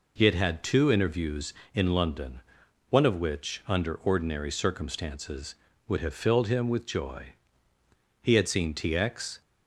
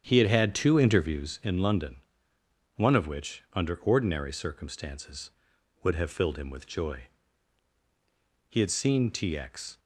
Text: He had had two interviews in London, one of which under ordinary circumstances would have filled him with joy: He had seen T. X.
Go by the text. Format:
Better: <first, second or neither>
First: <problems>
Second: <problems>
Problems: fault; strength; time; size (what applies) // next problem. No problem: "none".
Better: first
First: none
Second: starts louder than the rest; strong; until 1.3 s; 8.5 dB